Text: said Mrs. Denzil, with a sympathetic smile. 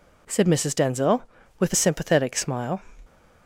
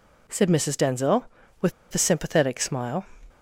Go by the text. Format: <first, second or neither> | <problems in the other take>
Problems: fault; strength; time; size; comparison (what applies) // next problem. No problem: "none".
first | pauses between "with" and "a"; slight; at 1.7 s; 0.20 s long